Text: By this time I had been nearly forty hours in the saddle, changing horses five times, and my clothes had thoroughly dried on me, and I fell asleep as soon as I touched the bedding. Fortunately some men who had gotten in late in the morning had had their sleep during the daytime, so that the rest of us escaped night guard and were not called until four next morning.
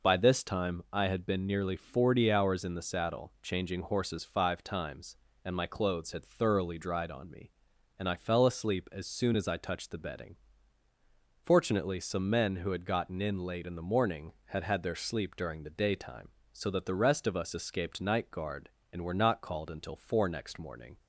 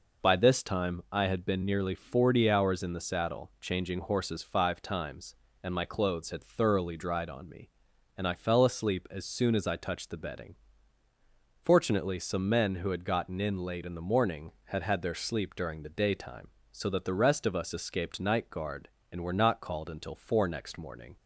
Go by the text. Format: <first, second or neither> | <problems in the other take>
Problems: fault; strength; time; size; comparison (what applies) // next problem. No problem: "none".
neither | none